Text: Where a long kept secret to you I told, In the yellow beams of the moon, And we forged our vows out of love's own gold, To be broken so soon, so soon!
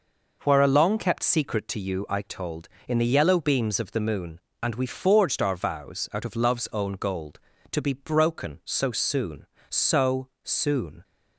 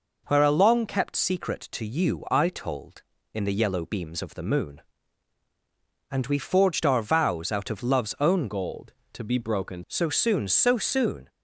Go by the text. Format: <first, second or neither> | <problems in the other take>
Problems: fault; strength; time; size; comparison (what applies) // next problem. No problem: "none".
first | changes voice from "gold" to "broken"; from 8.4 to 9.8 s; 1.4 s long